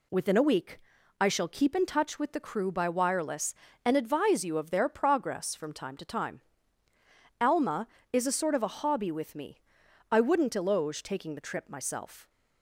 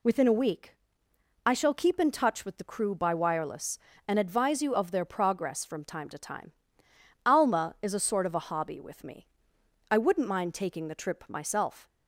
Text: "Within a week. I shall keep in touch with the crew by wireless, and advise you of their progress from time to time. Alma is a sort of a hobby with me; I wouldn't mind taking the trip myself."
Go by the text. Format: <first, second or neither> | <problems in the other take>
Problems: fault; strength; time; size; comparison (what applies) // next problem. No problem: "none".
second | says "eloge" for "mind"; at 10.5 s